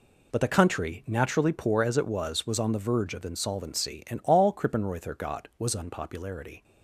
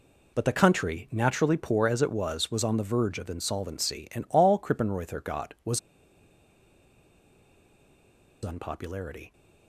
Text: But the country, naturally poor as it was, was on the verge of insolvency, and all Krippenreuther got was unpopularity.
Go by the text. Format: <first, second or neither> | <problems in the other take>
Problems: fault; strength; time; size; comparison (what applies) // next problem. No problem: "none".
first | pauses between "was" and "unpopularity"; strong; at 5.7 s; 2.6 s long